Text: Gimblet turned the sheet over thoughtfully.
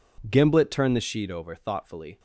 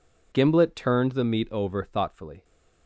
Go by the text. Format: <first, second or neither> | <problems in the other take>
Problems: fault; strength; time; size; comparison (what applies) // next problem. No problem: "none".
first | says "meat" for "sheet"; at 1.2 s